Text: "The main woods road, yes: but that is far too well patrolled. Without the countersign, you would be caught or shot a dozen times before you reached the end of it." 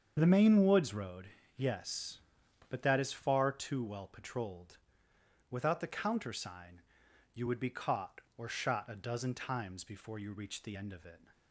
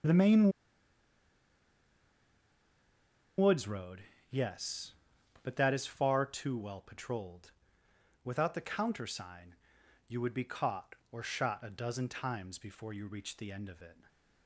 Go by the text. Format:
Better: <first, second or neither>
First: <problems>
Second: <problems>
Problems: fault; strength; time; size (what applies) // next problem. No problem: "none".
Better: first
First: starts louder than the rest; until 1.1 s; 7 dB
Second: starts louder than the rest; until 3.9 s; 7 dB // pauses between "main" and "woods"; strong; at 0.5 s; 2.8 s long